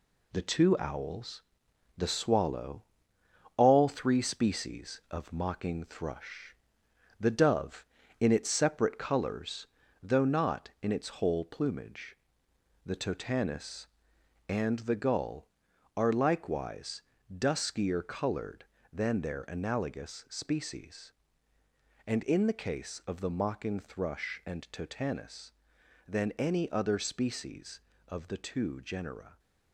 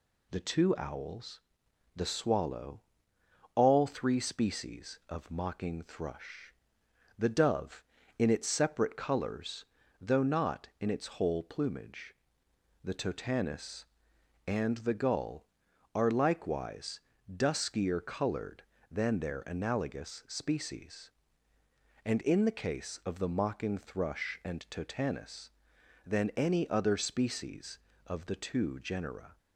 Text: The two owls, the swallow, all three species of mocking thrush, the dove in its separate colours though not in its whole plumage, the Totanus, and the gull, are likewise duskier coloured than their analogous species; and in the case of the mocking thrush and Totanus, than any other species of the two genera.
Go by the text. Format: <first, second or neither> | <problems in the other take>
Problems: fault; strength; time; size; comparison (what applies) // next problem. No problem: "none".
second | gets quieter; noticeable; throughout; 6 dB // pauses between "colours" and "though"; slight; at 9.6 s; 0.34 s long; slight in the second // pauses between "likewise" and "duskier"; slight; at 17.0 s; 0.34 s long; slight in the second